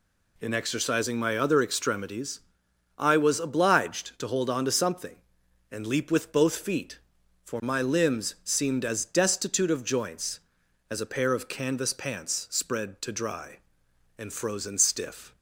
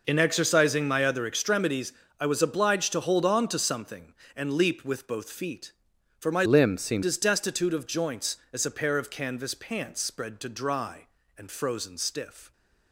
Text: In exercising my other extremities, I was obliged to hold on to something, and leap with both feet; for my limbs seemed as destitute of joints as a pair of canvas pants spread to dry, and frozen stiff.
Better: first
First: none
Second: changes voice from "limbs" to "seemed"; from 6.4 to 7.0 s; 0.6 s long

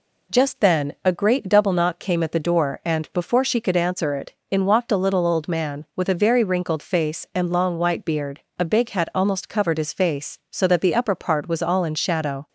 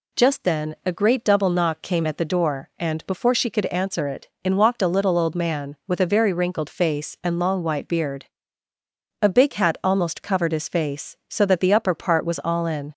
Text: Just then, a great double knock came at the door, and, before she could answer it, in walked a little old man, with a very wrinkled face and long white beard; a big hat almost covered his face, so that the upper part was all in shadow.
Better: first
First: none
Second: stops before "shadow"; at 12.9 s

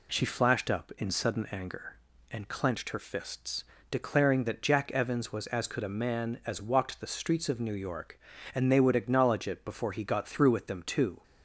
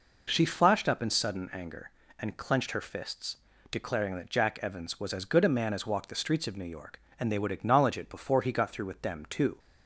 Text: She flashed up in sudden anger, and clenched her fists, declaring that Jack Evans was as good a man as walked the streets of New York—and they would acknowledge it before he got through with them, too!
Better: second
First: says "could" for "good"; at 5.6 s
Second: none

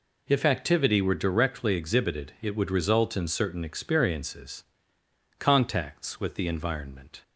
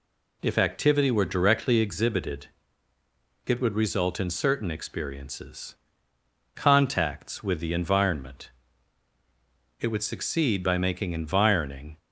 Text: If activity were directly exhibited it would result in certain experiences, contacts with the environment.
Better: first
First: none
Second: pauses between "exhibited" and "it"; at 2.4 s; 1.0 s long // goes on to say "It would succeed by making environing"; strong; from 9.7 s on; 2.1 s long

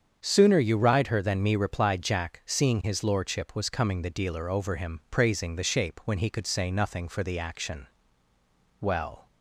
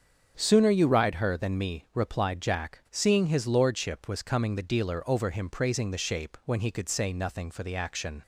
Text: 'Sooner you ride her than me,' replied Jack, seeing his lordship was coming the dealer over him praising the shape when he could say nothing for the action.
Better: second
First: starts louder than the rest; strong; until 1.2 s; 7.5 dB // goes on to say "Well"; slight; from 8.7 s on; 0.48 s long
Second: starts louder than the rest; strong; until 1.4 s; 7.5 dB

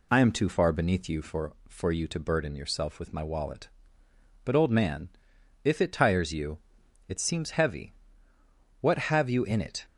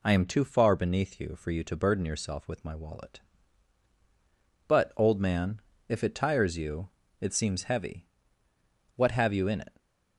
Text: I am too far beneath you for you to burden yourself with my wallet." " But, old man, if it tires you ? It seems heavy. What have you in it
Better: second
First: says "for" twice; at 1.6 s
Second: none

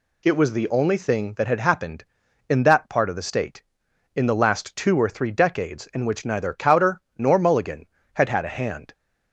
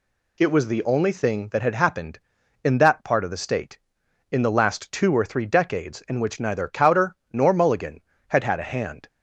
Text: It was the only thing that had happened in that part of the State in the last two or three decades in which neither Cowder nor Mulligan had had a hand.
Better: neither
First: pauses between "Cowder" and "nor"; slight; at 7.0 s; 0.16 s long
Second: pauses between "Cowder" and "nor"; slight; at 7.1 s; 0.16 s long

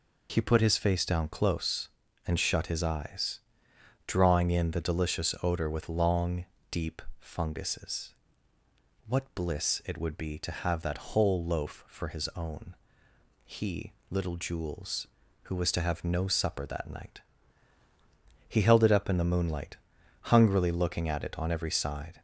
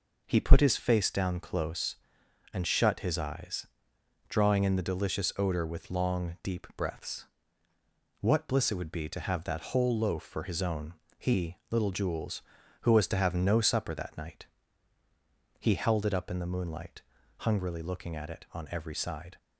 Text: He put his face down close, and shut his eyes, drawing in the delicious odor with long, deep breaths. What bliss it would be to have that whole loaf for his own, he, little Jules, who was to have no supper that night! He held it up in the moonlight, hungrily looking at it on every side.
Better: second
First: says "funguses" for "breaths"; at 7.1 s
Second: none

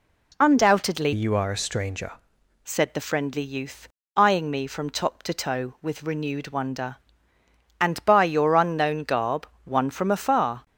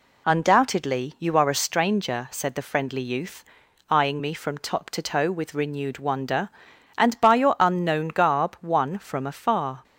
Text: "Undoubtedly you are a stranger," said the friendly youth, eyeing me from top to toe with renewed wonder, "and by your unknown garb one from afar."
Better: second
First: changes voice from "you" to "stranger"; from 1.1 to 2.1 s; 1.0 s long // pauses between "garb" and "one"; slight; at 9.4 s; 0.16 s long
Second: none

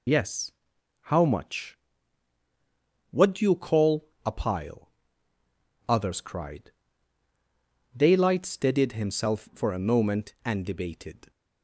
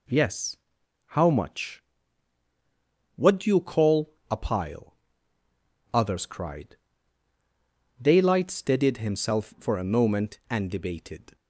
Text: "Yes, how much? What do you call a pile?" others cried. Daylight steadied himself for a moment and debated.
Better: second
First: loses the start of "Yes"; at 0.0 s; 40 ms // pauses between "call" and "a"; slight; at 4.0 s; 0.18 s long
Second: pauses between "call" and "a"; slight; at 4.1 s; 0.18 s long

